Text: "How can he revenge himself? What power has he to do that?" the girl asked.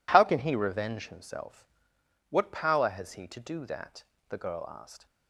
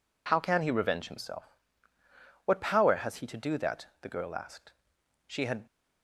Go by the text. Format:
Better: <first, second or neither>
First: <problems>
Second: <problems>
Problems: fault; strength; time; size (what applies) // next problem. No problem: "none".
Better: first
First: none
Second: goes on to say "She had"; slight; from 5.2 s on; 0.38 s long